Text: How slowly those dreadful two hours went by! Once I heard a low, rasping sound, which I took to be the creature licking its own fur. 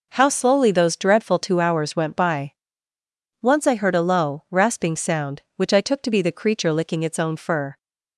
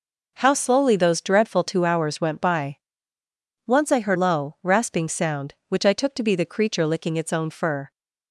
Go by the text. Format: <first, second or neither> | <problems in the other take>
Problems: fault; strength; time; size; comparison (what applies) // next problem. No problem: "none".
first | skips "a"; at 4.1 s